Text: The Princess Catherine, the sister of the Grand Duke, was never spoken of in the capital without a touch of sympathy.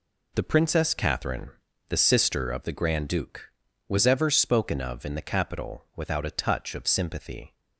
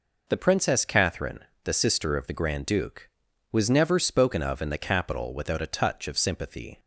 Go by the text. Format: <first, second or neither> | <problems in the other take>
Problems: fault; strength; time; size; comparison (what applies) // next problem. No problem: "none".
second | says "ever" for "never"; at 4.0 s